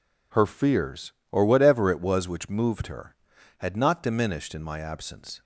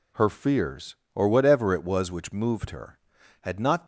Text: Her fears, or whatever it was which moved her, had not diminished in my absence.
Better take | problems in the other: first | stops before "diminished in my absence"; at 3.8 s

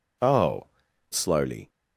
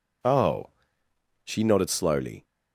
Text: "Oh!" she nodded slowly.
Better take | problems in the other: second | skips "she nodded"; at 0.8 s

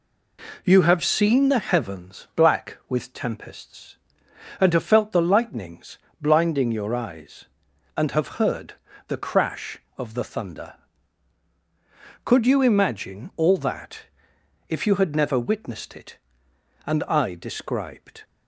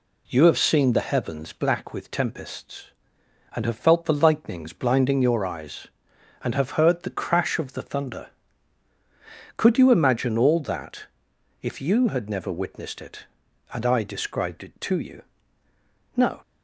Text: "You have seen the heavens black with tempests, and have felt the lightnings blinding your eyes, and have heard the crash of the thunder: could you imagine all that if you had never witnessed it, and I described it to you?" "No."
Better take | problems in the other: second | pauses between "lightnings" and "blinding"; slight; at 5.9 s; 0.24 s long // pauses between "heard" and "the"; slight; at 8.7 s; 0.36 s long // pauses between "that" and "if"; noticeable; at 14.0 s; 0.66 s long; noticeable in the second // stops before "it to you No"; at 18.2 s

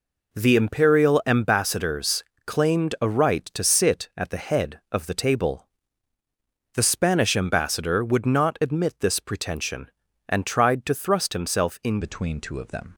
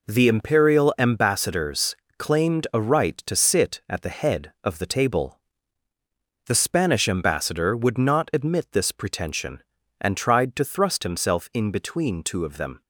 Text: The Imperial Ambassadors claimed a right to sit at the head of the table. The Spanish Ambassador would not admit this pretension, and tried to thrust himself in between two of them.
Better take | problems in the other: second | pauses between "Ambassadors" and "claimed"; slight; at 2.2 s; 0.22 s long; slight in the second // changes voice at "between"; from 12.0 s on; 0.9 s long

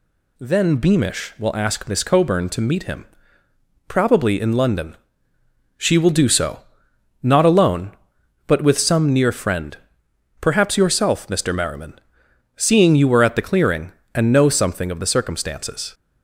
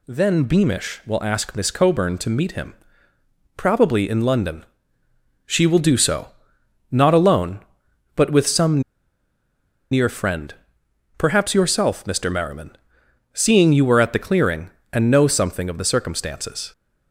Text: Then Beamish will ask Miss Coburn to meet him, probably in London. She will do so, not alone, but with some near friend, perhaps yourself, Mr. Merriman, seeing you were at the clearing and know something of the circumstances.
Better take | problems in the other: first | pauses between "some" and "near"; at 8.8 s; 1.0 s long

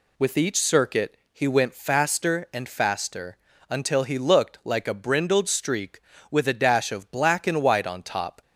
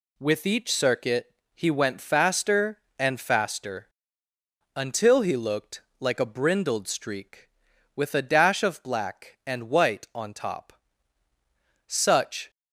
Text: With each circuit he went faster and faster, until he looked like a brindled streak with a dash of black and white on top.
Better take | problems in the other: first | pauses between "circuit" and "he"; slight; at 1.3 s; 0.20 s long // pauses between "looked" and "like"; slight; at 5.8 s; 0.18 s long // goes on to say "Such"; noticeable; from 11.8 s on; 0.64 s long

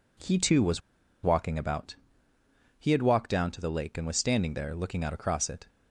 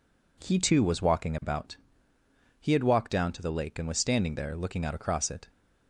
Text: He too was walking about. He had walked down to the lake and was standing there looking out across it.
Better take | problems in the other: second | pauses between "was" and "walking"; at 0.8 s; 0.43 s long

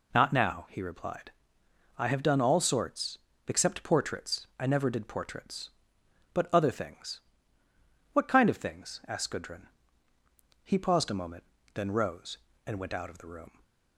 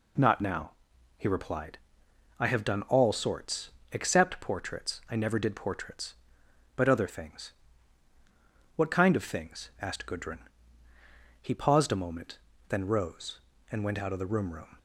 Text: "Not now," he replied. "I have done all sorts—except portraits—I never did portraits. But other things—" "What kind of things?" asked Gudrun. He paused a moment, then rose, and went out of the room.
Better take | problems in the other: first | says "room" twice; at 14.5 s

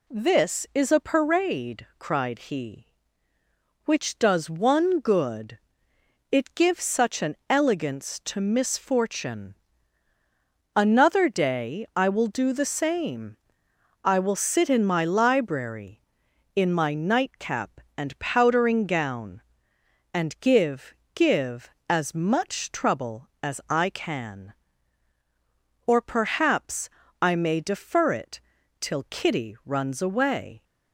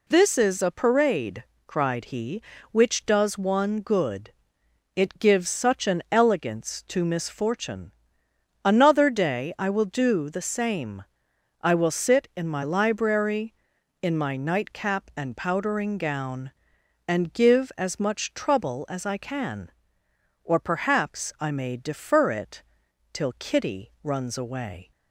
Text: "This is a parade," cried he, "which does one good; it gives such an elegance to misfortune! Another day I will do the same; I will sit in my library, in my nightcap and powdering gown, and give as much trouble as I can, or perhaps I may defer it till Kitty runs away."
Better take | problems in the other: second | says "give" twice; at 21.1 s // pauses between "perhaps" and "I"; slight; at 26.8 s; 0.32 s long // pauses between "it" and "till"; at 28.3 s; 0.40 s long; noticeable in the second

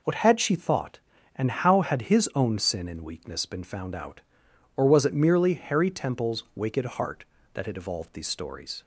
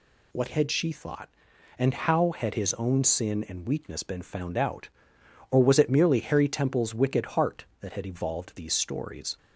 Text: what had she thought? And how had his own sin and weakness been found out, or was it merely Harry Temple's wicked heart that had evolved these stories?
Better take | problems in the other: neither | none

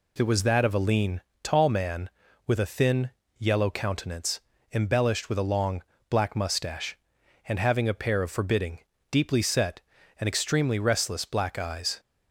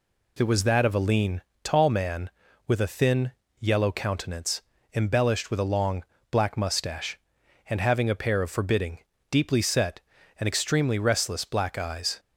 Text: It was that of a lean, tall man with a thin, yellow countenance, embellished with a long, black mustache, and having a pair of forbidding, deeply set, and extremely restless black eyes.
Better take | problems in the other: neither | none

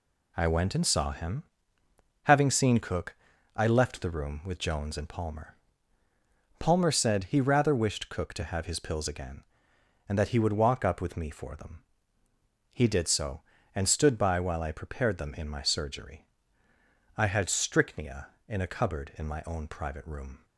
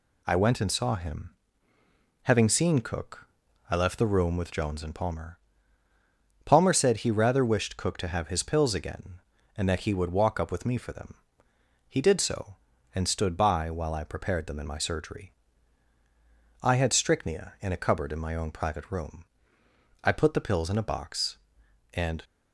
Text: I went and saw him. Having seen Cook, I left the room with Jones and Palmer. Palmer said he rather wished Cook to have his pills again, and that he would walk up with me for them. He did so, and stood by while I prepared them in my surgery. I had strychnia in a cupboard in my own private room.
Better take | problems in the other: first | goes on to say "I put the pills in a box and"; strong; from 20.0 s on; 2.2 s long

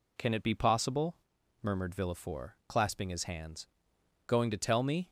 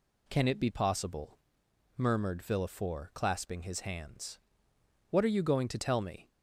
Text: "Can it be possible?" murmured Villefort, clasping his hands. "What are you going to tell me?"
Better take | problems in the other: second | skips "What are you"; at 3.9 s

